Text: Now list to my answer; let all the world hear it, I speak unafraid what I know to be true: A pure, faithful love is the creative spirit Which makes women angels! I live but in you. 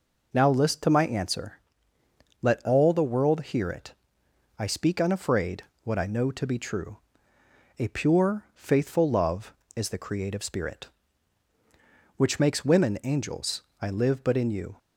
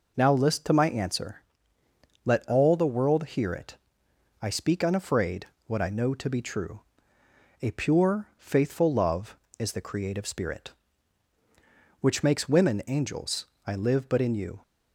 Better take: neither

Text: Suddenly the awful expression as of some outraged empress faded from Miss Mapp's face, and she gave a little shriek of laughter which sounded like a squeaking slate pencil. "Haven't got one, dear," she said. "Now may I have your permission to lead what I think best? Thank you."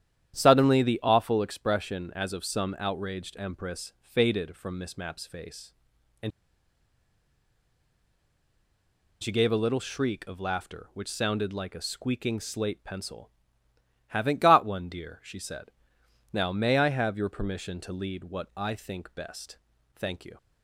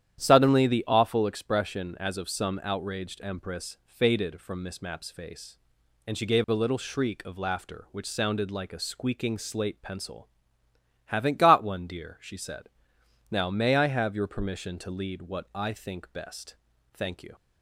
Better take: second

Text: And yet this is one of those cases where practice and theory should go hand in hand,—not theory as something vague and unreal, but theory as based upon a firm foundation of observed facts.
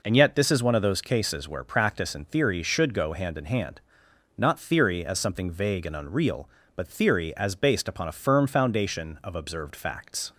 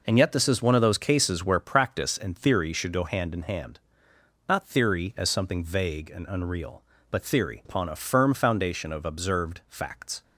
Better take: first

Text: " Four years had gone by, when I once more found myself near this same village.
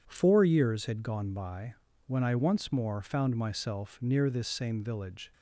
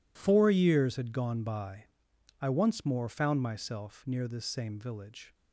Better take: first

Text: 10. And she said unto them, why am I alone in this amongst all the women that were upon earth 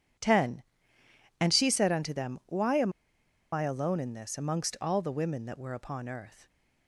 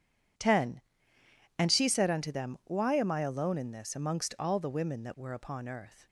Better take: second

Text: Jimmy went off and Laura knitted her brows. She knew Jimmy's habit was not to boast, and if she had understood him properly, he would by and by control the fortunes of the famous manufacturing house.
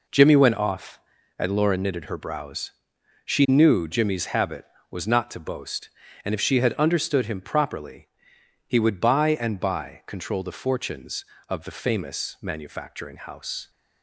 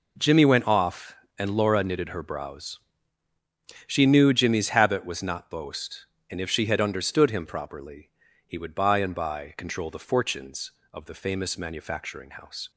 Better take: first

